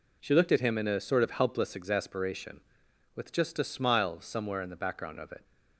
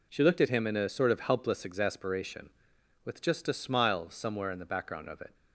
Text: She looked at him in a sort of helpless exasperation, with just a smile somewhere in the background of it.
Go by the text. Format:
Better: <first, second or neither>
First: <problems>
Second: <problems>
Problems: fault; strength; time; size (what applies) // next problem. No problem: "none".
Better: neither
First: none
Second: none